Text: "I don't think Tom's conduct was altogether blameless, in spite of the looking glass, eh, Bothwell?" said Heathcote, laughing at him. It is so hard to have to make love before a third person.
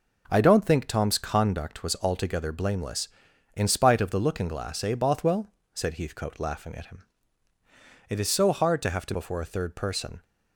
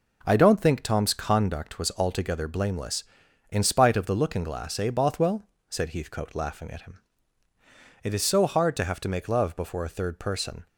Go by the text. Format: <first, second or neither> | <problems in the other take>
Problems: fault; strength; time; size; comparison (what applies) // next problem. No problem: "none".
second | skips "make love"; at 9.1 s